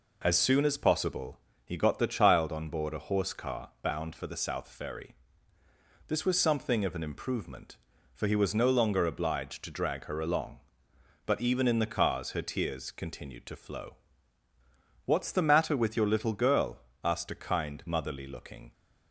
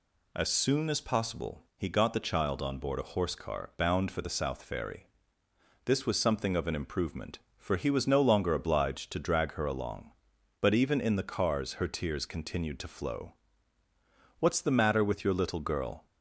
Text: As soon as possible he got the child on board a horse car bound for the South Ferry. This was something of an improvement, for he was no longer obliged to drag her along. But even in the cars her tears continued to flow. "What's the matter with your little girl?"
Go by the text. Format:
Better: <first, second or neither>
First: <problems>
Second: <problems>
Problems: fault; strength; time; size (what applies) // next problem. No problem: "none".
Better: second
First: pauses between "possible" and "he"; slight; at 1.3 s; 0.26 s long // goes on to say "asked a kind motherly looking"; strong; from 17.0 s on; 1.7 s long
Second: none